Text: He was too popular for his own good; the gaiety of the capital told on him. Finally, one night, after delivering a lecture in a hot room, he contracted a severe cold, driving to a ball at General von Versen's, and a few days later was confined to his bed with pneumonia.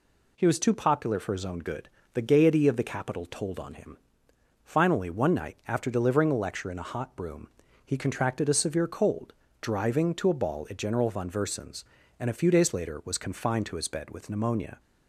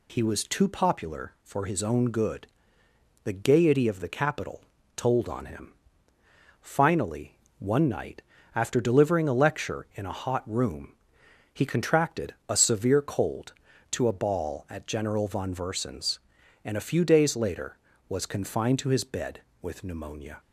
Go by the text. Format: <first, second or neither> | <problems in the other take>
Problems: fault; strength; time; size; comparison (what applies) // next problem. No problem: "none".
first | pauses between "capital" and "told"; slight; at 4.6 s; 0.36 s long // skips "driving"; at 13.7 s